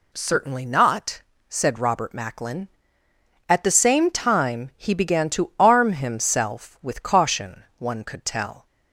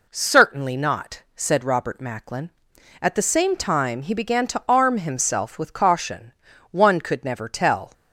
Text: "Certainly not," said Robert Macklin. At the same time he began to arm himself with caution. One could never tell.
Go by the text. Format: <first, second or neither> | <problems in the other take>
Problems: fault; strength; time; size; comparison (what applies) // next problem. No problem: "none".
second | skips "never"; at 8.2 s